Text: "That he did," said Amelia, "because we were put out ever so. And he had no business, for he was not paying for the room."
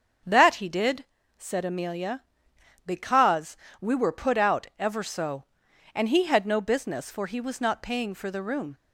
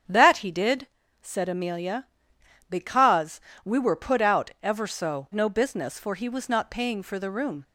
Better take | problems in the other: first | starts louder than the rest; strong; until 1.4 s; 8.5 dB; strong in the first // pauses between "because" and "we"; slight; at 3.3 s; 0.24 s long; slight in the first // skips "And he had"; at 5.3 s

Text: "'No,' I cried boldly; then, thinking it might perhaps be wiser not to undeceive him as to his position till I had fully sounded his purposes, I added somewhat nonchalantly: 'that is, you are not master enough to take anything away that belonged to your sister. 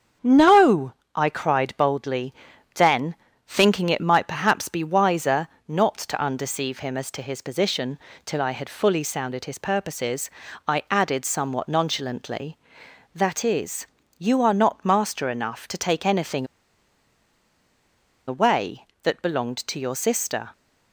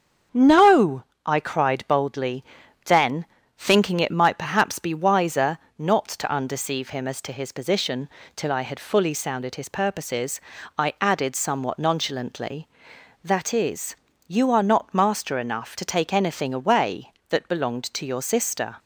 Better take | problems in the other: second | starts louder than the rest; strong; until 1.4 s; 7.5 dB; strong in the second // pauses between "wiser" and "not"; slight; at 5.4 s; 0.18 s long; slight in the second // pauses between "position" and "till"; slight; at 7.9 s; 0.28 s long; slight in the second // pauses between "anything" and "away"; strong; at 16.4 s; 1.8 s long

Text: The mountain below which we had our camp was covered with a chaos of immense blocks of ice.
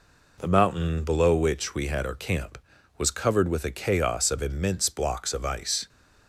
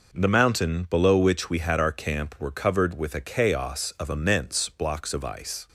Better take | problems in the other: first | says "were" for "was"; at 2.3 s

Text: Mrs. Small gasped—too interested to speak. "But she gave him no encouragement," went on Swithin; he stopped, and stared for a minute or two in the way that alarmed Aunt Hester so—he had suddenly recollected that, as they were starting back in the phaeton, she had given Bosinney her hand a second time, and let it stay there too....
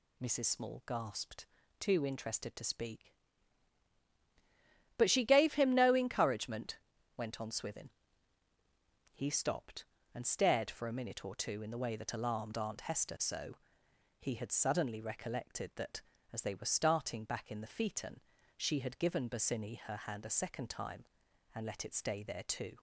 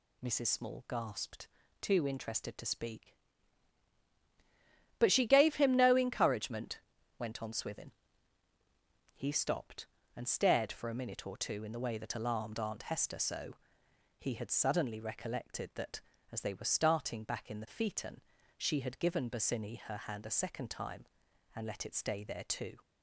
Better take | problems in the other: neither | none

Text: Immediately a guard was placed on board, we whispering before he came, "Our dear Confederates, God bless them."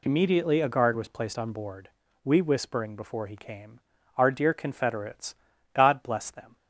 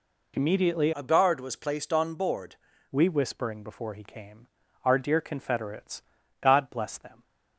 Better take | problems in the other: first | changes voice from "a" to "board"; from 0.9 to 2.5 s; 1.6 s long

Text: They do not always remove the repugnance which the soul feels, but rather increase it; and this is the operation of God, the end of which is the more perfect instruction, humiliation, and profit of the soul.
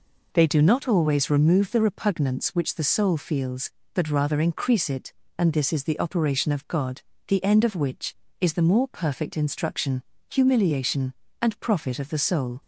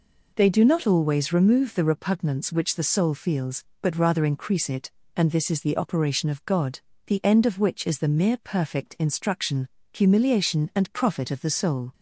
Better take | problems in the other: first | says "mere" for "more"; at 8.0 s

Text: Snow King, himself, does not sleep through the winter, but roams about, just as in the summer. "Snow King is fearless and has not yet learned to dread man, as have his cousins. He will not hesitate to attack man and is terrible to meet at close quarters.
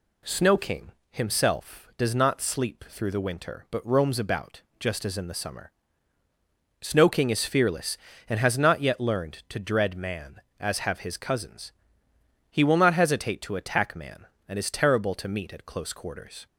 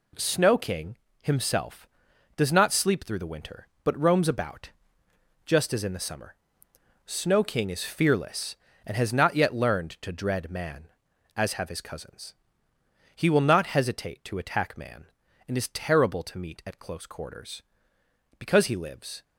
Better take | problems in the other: first | goes on to say "Because he lives"; noticeable; from 18.3 s on; 0.86 s long

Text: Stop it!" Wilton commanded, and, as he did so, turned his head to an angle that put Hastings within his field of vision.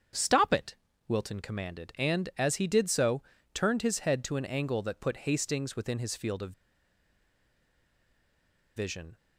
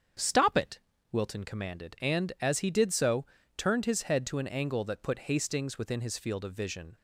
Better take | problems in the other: second | starts louder than the rest; strong; until 1.4 s; 7.5 dB; strong in the second // pauses between "of" and "vision"; strong; at 6.5 s; 2.2 s long

